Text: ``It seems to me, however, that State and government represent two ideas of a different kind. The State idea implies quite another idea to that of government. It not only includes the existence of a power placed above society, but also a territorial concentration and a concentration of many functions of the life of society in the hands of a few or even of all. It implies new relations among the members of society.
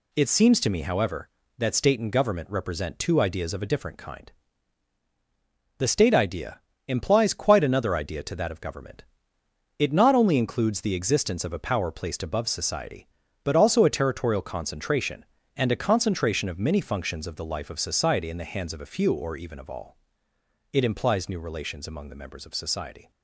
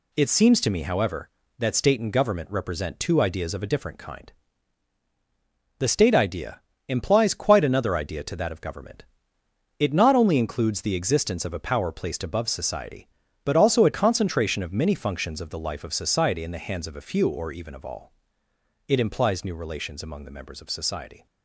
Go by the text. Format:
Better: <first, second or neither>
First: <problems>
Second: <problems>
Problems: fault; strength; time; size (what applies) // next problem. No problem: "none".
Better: first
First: pauses between "idea" and "implies"; slight; at 6.5 s; 0.26 s long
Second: pauses between "idea" and "implies"; slight; at 6.6 s; 0.26 s long // skips "territorial concentration and a"; at 13.9 s